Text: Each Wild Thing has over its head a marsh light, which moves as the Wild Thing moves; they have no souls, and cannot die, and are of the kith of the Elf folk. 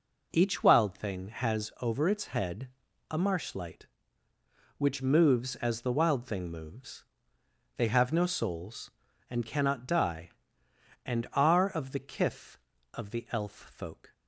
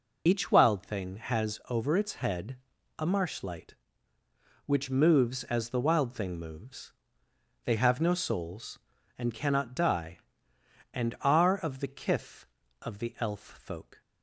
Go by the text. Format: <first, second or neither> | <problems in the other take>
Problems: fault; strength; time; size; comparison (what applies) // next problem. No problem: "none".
first | loses the start of "Each"; at 0.2 s; 50 ms // pauses between "head" and "a"; at 2.5 s; 0.42 s long; also in the first